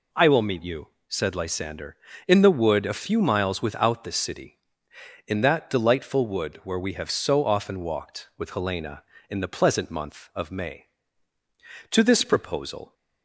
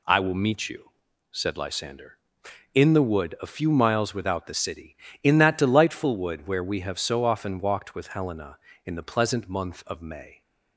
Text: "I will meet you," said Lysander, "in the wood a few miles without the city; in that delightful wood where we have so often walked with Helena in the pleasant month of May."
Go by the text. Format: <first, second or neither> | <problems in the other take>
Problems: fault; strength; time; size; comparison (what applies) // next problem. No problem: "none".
second | goes on to say "To this proposal"; noticeable; from 11.9 s on; 1.0 s long